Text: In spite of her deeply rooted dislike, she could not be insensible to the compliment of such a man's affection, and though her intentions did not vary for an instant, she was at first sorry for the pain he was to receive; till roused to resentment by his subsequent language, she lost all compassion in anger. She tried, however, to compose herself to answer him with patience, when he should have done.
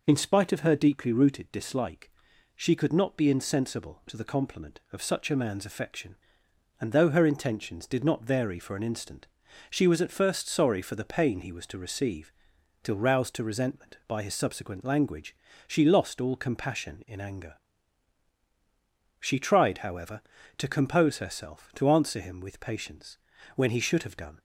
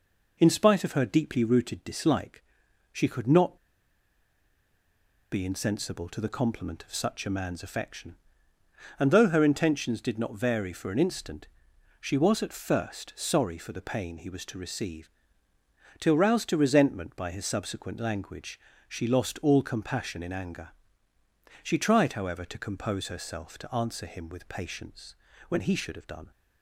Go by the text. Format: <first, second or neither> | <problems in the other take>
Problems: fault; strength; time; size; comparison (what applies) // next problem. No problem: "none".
first | pauses between "not" and "be"; strong; at 3.5 s; 1.7 s long